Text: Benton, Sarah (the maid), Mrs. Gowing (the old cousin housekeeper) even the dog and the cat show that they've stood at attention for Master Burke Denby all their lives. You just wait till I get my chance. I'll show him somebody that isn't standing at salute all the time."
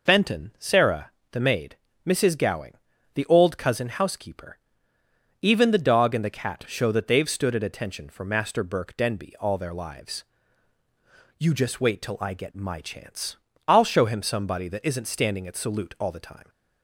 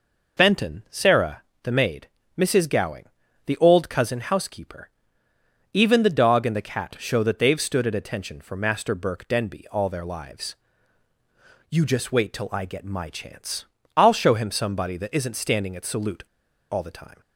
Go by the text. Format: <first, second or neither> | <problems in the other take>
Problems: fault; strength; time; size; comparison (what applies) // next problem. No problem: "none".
first | pauses between "salute" and "all"; noticeable; at 16.2 s; 0.48 s long